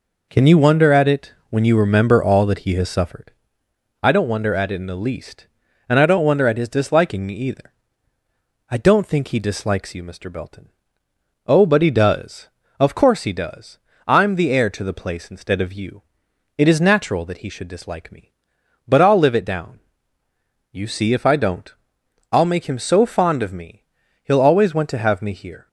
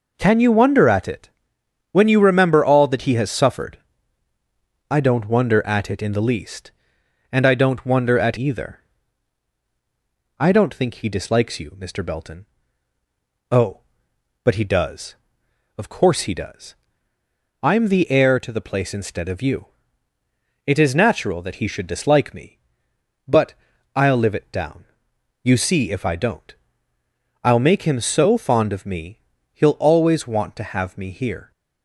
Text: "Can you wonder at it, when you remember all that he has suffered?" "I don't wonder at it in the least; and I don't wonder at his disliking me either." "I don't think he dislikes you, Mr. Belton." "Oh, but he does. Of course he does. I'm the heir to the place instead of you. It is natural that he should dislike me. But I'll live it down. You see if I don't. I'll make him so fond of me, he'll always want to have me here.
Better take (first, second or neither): first